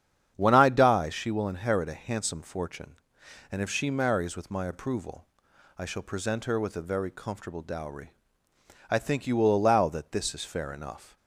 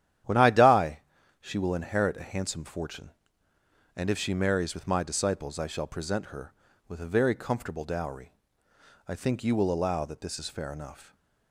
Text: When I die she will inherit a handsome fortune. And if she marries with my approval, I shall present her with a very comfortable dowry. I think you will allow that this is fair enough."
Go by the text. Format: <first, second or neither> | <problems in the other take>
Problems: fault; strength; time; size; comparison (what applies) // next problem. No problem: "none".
first | starts louder than the rest; strong; until 1.6 s; 11 dB; strong in the first // pauses between "die" and "she"; at 0.9 s; 0.40 s long // says "disciples" for "approval"; at 5.0 s